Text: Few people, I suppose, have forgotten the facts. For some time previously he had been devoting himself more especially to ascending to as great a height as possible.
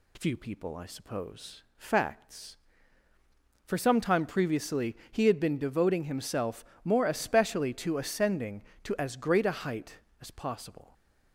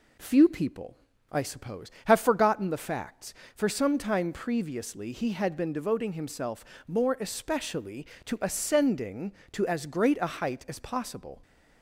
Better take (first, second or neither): second